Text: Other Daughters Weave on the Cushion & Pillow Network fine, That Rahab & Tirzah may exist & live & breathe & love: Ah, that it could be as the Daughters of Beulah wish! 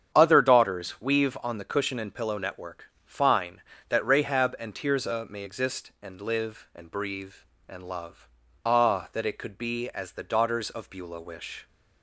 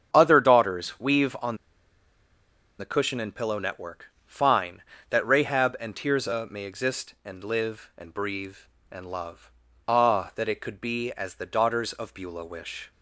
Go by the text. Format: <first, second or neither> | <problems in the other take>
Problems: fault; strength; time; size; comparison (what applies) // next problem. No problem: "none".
first | starts louder than the rest; strong; until 1.1 s; 8 dB; strong in the first // pauses between "on" and "the"; at 1.5 s; 1.2 s long // pauses between "Network" and "fine"; slight; at 4.1 s; 0.16 s long; slight in the first